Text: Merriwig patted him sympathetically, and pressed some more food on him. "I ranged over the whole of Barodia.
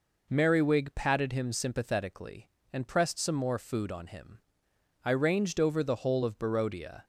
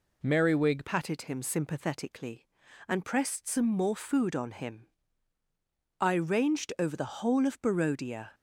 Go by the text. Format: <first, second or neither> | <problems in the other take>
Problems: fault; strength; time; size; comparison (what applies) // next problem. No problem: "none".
first | changes voice at "patted"; from 0.8 s on; 7.5 s long